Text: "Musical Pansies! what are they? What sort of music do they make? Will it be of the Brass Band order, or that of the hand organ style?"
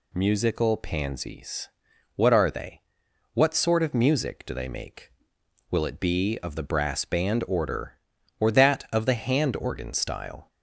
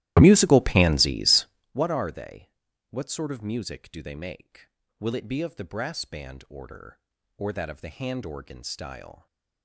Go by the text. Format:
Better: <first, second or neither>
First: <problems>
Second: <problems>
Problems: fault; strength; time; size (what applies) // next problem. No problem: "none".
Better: first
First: none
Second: starts louder than the rest; strong; until 1.7 s; 15 dB